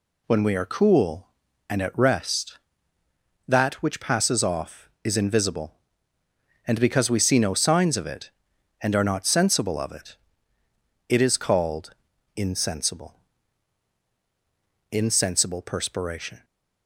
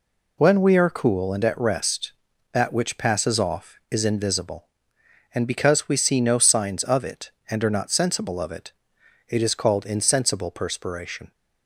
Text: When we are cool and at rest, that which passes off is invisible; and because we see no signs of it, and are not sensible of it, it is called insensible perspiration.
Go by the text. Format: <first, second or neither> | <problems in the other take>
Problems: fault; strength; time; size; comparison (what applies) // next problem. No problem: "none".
second | pauses between "called" and "insensible"; at 11.9 s; 0.42 s long // says "insensible" twice; at 14.9 s